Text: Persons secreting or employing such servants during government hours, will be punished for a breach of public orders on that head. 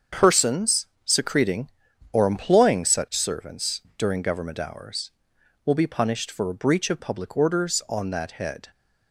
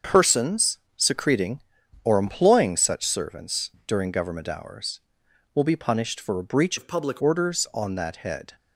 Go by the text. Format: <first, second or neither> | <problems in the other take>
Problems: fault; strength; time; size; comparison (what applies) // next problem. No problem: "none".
first | starts louder than the rest; until 1.2 s; 6.5 dB; also in the first // pauses between "Persons" and "secreting"; slight; at 0.7 s; 0.18 s long; slight in the first // pauses between "servants" and "during"; slight; at 3.7 s; 0.16 s long; slight in the first // changes voice from "of" to "public"; from 6.7 to 7.1 s; 0.4 s long